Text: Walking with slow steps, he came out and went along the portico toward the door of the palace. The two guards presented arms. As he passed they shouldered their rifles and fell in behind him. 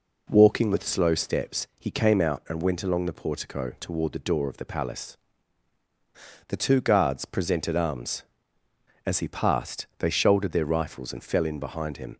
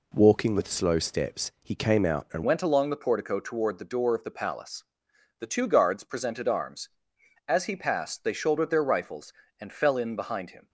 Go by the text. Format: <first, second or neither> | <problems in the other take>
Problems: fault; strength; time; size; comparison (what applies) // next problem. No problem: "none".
first | changes voice at "went"; from 2.4 s on; 8.2 s long